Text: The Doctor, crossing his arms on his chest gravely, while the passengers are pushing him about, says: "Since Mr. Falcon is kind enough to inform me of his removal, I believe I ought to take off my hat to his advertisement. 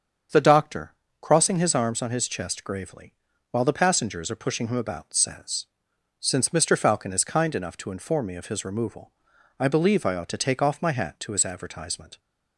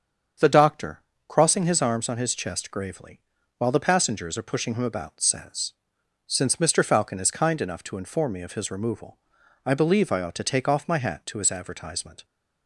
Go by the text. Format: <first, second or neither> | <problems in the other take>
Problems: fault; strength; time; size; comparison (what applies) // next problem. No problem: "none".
neither | starts louder than the rest; strong; the same in both